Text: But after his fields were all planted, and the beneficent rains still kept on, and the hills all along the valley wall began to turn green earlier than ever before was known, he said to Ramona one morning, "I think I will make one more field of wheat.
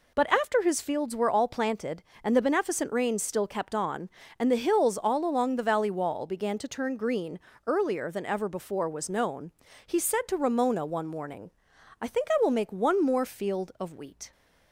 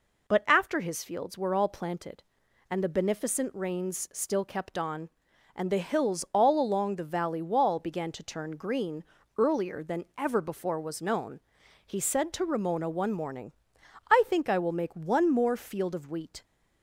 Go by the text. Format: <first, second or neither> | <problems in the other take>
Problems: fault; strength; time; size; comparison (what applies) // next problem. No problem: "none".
neither | pauses between "green" and "earlier"; slight; the same in both